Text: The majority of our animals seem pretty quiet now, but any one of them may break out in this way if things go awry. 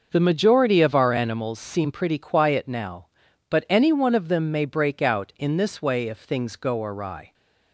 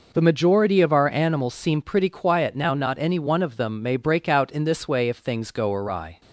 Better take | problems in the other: first | says "not" for "but"; at 2.7 s

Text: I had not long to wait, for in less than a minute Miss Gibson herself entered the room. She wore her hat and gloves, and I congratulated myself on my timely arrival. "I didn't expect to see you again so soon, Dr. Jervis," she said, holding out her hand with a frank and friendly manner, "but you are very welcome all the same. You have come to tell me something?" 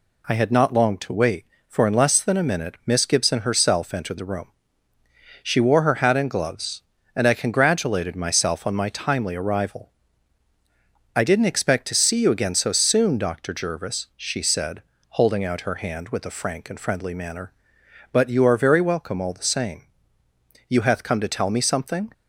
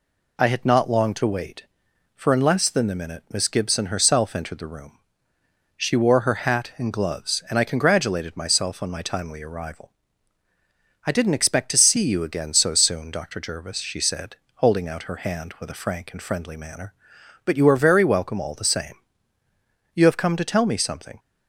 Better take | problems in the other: second | says "hath" for "have"; at 20.8 s

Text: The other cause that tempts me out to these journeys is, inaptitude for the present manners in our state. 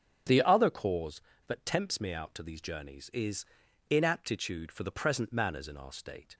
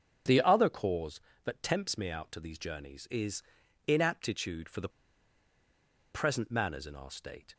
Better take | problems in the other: first | starts louder than the rest; strong; until 1.5 s; 7 dB; strong in the first // pauses between "the" and "present"; at 4.8 s; 1.2 s long

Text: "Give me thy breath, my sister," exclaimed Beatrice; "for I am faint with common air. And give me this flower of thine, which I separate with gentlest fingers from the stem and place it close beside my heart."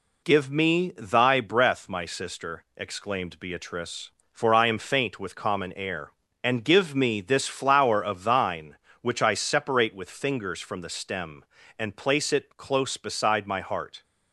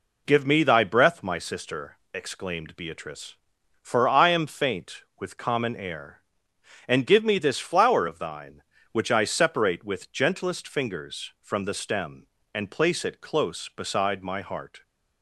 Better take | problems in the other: second | skips "gentlest"; at 10.0 s

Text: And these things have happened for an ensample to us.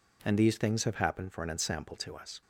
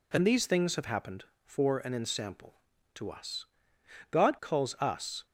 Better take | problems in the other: first | goes on to say "God calls us"; noticeable; from 4.1 s on; 1.1 s long

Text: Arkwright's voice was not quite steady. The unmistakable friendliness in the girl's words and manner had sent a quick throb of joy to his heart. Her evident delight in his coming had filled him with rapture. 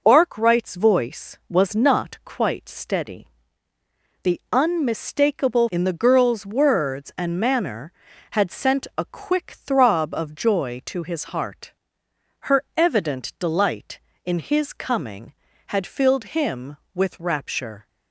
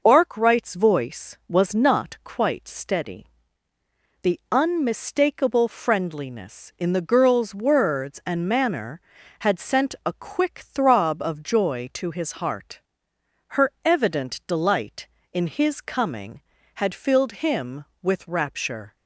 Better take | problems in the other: second | skips "friendliness"; at 5.6 s // pauses between "Her" and "evident"; slight; at 12.6 s; 0.16 s long; slight in the second

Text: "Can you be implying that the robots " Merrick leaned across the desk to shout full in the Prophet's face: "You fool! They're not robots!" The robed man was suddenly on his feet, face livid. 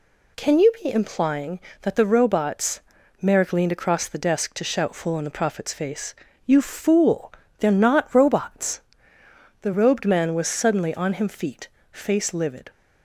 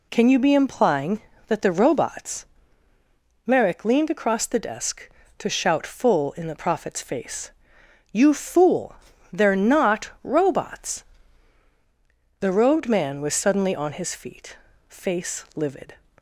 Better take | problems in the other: second | says "him" for "his"; at 11.1 s

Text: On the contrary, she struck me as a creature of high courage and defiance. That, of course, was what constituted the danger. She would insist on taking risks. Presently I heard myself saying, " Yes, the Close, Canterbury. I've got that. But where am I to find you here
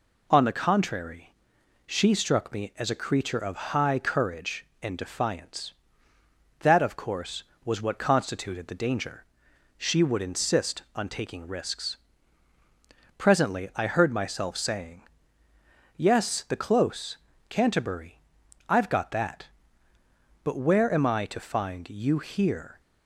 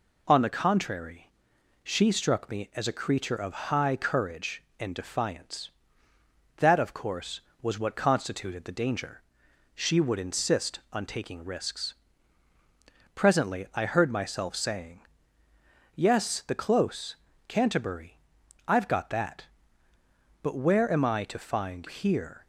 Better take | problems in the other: first | skips "you"; at 21.8 s

